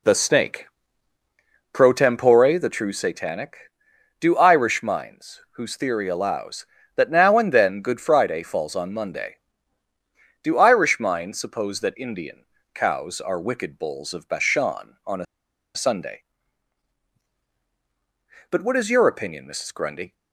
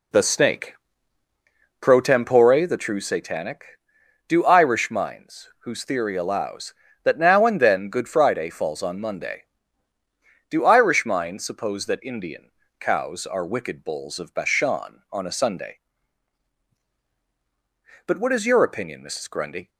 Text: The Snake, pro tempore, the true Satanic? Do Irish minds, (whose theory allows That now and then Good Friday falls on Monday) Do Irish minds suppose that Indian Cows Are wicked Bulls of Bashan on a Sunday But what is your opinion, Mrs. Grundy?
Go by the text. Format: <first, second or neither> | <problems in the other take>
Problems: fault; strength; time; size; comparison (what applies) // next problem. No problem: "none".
second | pauses between "Indian" and "Cows"; slight; at 12.4 s; 0.30 s long; slight in the second // pauses between "a" and "Sunday"; noticeable; at 15.2 s; 0.49 s long